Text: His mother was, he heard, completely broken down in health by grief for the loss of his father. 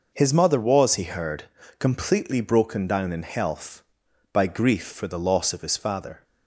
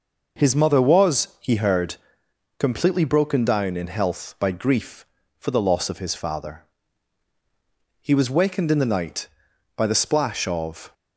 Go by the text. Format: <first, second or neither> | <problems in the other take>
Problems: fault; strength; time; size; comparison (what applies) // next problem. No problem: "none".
first | goes on to say "He was wakened in the night by the splash of"; strong; from 8.0 s on; 2.9 s long